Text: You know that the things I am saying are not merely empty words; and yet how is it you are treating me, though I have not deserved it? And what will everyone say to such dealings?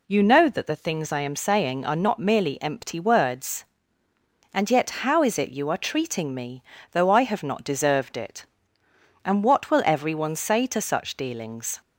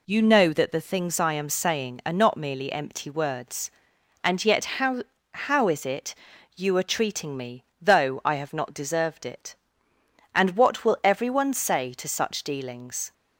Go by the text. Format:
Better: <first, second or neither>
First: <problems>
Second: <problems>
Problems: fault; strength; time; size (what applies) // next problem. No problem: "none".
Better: first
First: none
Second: says "how" twice; at 5.3 s // pauses between "it" and "you"; at 6.1 s; 0.42 s long